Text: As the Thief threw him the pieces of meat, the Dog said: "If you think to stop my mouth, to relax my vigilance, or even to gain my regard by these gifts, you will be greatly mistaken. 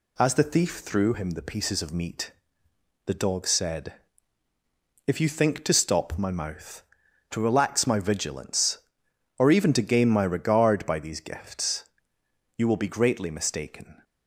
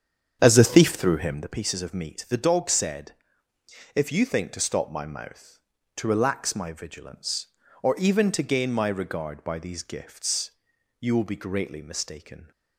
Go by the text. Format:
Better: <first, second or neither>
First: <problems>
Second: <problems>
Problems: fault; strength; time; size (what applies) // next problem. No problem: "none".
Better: first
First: none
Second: starts louder than the rest; strong; until 1.6 s; 8 dB